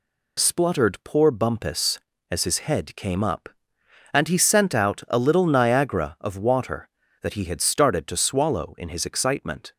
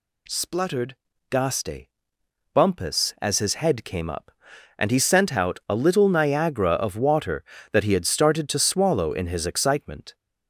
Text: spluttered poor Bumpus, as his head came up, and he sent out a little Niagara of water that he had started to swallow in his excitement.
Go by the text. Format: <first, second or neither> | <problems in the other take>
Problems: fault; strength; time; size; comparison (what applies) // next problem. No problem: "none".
first | says "gaste" for "poor"; at 1.3 s